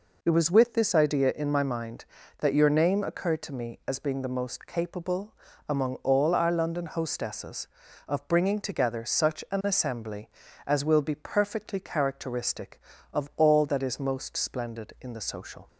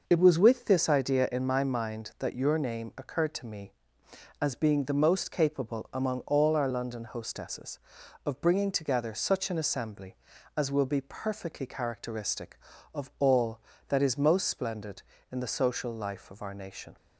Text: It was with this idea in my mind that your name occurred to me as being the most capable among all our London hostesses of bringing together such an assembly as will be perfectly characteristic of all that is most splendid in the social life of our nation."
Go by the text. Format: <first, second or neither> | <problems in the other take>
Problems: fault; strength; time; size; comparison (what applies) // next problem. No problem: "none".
second | pauses between "capable" and "among"; slight; at 5.3 s; 0.34 s long // stops before "life of our nation"; at 15.6 s